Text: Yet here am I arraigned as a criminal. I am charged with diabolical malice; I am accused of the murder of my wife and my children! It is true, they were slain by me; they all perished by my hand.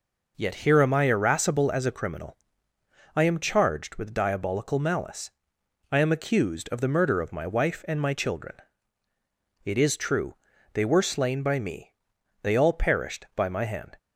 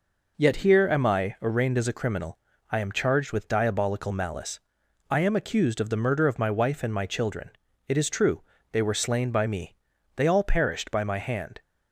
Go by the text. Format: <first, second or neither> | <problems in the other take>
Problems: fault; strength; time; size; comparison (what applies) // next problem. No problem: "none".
second | says "irascible" for "arraigned"; at 1.0 s